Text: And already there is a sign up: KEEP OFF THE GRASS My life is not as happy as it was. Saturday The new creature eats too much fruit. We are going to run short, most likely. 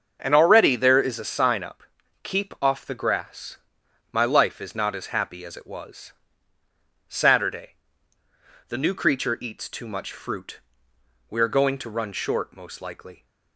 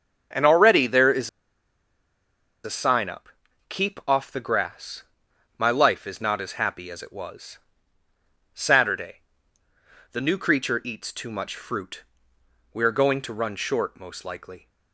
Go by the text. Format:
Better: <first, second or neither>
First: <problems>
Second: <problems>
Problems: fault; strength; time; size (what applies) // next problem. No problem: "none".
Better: first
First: starts louder than the rest; until 1.2 s; 7 dB // pauses between "GRASS" and "My"; noticeable; at 3.5 s; 0.56 s long // pauses between "Saturday" and "The"; at 7.7 s; 0.98 s long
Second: starts louder than the rest; until 2.6 s; 7 dB // pauses between "is" and "a"; strong; at 1.2 s; 1.3 s long // pauses between "GRASS" and "My"; noticeable; at 5.0 s; 0.56 s long // pauses between "Saturday" and "The"; noticeable; at 9.1 s; 0.96 s long